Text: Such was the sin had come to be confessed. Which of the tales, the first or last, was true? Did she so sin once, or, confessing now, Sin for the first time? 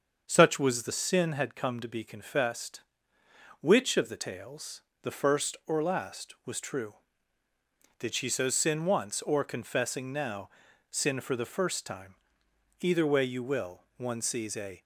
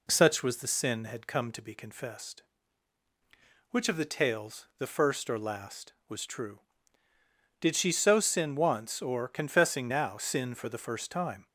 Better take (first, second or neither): second